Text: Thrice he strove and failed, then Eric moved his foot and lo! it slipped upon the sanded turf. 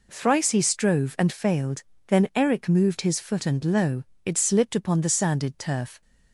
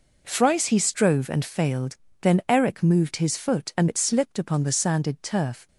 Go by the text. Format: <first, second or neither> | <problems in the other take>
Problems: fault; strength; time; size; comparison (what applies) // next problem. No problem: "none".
first | skips "lo"; at 3.8 s